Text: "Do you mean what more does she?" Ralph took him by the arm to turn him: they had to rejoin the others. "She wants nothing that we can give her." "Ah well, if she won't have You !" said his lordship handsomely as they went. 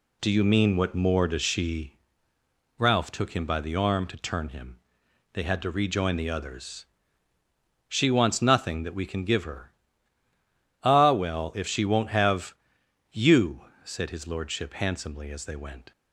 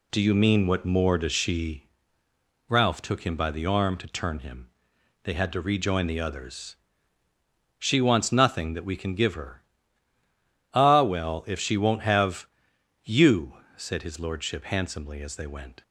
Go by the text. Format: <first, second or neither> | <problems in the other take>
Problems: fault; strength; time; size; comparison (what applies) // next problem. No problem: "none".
neither | pauses between "have" and "You"; noticeable; the same in both